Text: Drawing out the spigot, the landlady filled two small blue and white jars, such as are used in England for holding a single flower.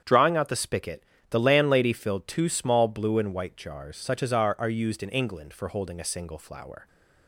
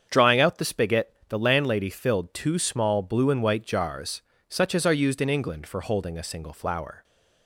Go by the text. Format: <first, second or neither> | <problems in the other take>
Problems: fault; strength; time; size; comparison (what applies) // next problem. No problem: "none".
second | starts louder than the rest; strong; until 1.3 s; 8 dB; strong in the second // says "are" twice; at 4.5 s